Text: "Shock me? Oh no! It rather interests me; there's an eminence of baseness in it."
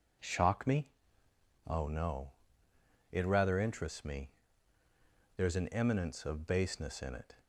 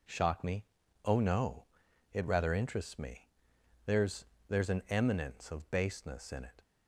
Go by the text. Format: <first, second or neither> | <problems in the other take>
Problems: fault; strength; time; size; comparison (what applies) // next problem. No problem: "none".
first | says "there's" twice; at 4.4 s